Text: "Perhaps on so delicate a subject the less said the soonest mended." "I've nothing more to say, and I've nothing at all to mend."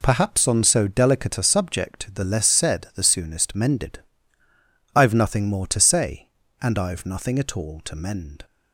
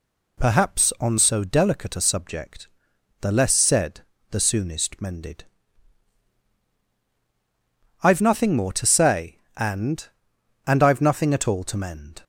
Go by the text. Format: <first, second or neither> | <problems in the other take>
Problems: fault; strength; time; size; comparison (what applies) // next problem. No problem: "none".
first | pauses between "subject" and "the"; noticeable; at 2.6 s; 0.54 s long // pauses between "said" and "the"; slight; at 4.0 s; 0.28 s long // says "and" twice; at 10.6 s